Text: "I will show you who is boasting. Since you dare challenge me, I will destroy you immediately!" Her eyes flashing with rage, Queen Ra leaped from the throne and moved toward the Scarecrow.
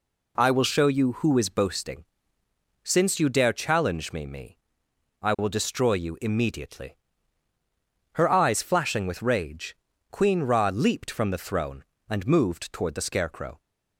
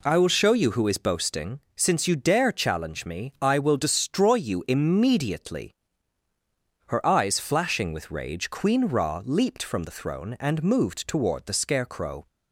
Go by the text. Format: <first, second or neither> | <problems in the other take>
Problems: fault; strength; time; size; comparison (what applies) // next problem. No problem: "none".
second | says "me" twice; at 4.2 s